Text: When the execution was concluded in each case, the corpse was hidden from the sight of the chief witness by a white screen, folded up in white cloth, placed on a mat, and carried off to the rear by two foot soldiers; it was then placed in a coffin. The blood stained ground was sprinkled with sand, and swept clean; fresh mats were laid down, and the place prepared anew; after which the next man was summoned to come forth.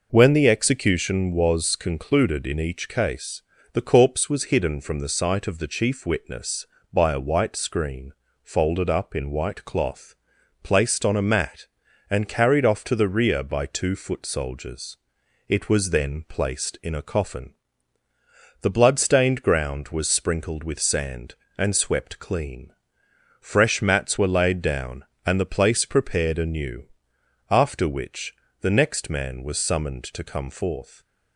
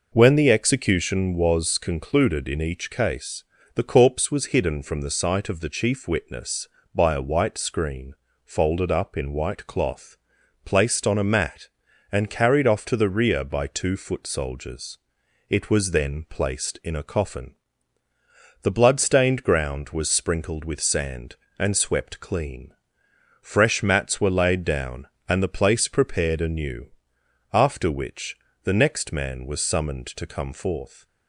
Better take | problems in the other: neither | pauses between "which" and "the"; slight; the same in both

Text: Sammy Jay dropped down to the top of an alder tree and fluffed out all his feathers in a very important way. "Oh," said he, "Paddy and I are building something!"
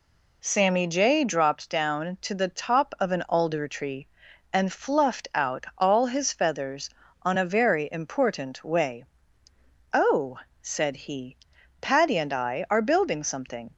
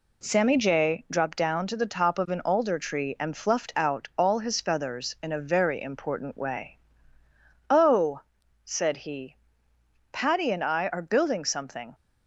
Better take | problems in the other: second | says "on" for "in"; at 7.2 s

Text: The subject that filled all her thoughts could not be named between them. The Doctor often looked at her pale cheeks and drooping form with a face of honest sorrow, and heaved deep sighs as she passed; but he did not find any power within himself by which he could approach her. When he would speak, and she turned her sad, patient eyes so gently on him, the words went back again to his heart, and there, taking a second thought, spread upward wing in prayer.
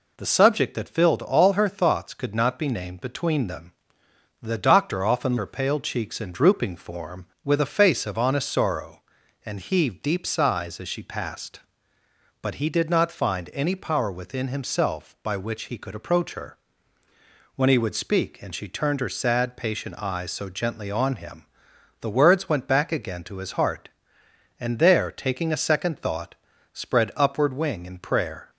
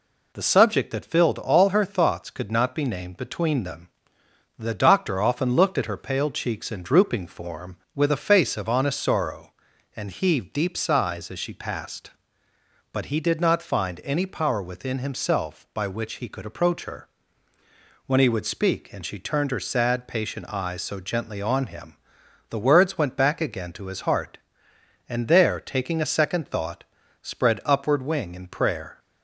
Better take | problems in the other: second | skips "looked at"; at 5.3 s

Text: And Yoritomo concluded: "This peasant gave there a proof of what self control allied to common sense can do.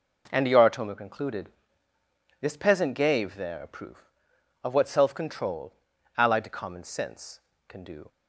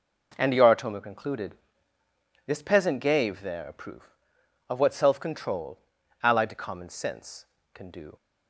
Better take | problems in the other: neither | pauses between "control" and "allied"; noticeable; the same in both

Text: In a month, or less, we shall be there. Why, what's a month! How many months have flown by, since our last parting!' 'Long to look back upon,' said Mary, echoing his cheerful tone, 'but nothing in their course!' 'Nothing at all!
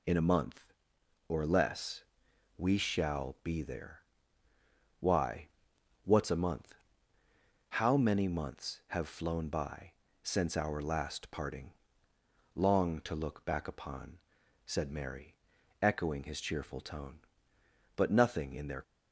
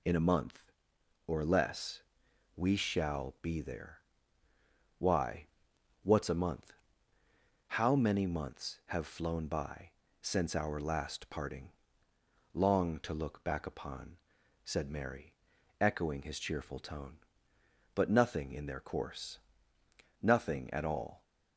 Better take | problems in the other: second | stops before "course Nothing at all"; at 18.8 s

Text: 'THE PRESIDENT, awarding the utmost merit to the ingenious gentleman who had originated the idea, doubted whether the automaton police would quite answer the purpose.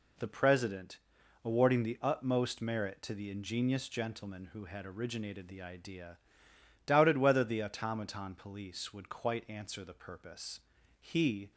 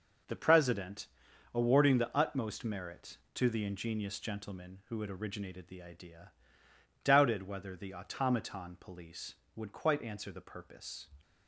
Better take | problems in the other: second | goes on to say "He"; from 10.9 s on; 0.52 s long

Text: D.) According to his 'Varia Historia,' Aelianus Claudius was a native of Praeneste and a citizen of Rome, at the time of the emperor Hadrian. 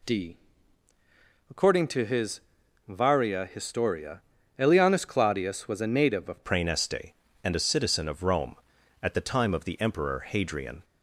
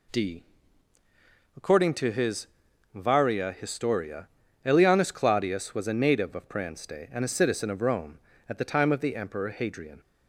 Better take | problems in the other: second | pauses between "his" and "Varia"; noticeable; at 2.4 s; 0.48 s long; noticeable in the second // changes voice at "Praeneste"; from 6.4 s on; 4.4 s long

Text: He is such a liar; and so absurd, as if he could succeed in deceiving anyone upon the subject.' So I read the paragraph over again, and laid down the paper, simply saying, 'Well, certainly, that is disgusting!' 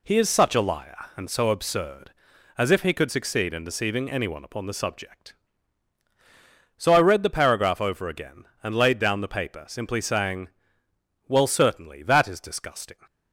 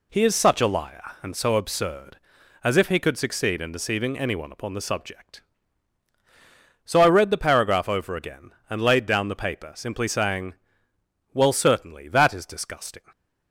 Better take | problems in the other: neither | none

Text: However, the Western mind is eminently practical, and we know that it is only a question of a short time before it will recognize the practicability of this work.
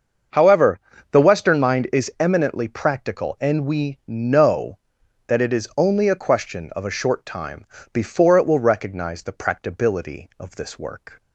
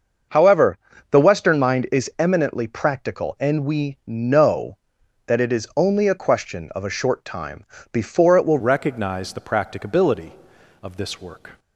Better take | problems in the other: first | starts louder than the rest; until 1.6 s; 6 dB; also in the first // pauses between "time" and "before"; slight; at 7.6 s; 0.28 s long; slight in the first // changes voice at "recognize"; from 8.5 s on; 3.0 s long

